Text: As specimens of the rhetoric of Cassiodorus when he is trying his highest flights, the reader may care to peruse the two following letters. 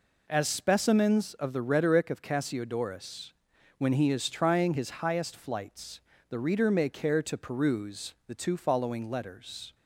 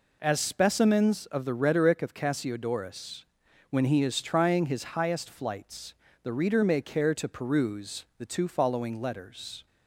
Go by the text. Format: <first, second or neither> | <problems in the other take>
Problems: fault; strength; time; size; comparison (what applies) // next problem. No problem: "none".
neither | pauses between "Cassiodorus" and "when"; noticeable; the same in both